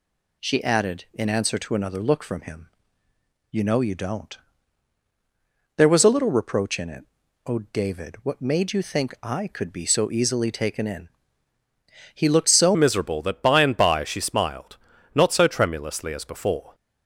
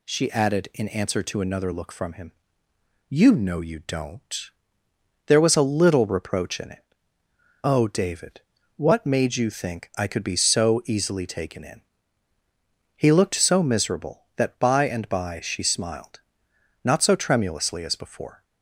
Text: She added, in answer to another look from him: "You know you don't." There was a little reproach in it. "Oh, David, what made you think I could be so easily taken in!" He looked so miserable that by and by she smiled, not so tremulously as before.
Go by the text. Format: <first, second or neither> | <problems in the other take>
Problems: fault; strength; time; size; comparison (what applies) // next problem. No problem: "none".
second | changes voice at "miserable"; from 12.7 s on; 4.0 s long